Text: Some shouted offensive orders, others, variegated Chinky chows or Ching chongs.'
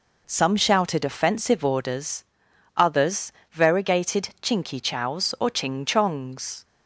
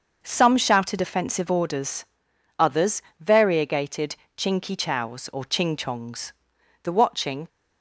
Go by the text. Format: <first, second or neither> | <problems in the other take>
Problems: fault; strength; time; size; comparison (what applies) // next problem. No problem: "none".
first | starts louder than the rest; until 1.2 s; 6.5 dB // pauses between "variegated" and "Chinky"; slight; at 4.1 s; 0.22 s long // goes on to say "The watching"; noticeable; from 6.8 s on; 0.64 s long